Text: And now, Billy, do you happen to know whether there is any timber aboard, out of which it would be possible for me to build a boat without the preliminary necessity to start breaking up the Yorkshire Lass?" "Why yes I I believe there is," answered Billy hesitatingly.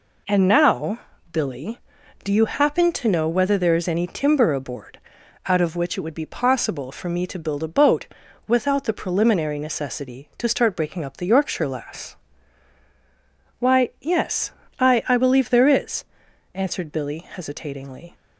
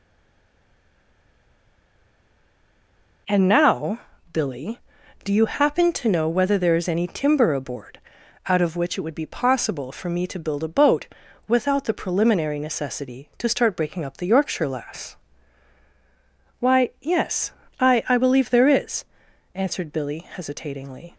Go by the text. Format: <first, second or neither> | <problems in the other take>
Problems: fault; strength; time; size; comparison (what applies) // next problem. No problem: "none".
first | stays silent before the first word; strong; until 3.2 s; 3.2 s long // pauses between "boat" and "without"; at 11.0 s; 0.40 s long; also in the first // pauses between "yes" and "I"; slight; at 17.5 s; 0.28 s long; slight in the first